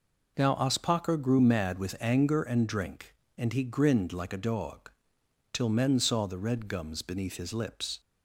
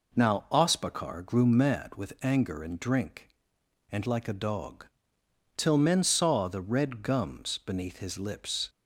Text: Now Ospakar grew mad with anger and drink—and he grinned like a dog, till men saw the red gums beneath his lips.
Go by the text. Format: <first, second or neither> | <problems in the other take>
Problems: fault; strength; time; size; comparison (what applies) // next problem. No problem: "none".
first | skips "he grinned"; at 4.0 s